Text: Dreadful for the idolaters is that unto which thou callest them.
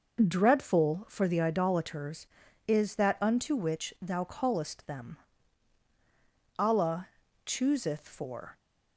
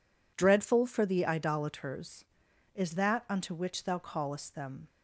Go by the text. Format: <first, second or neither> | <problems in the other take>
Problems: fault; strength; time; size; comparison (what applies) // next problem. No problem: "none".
second | goes on to say "Allah chooseth for"; strong; from 6.5 s on; 2.0 s long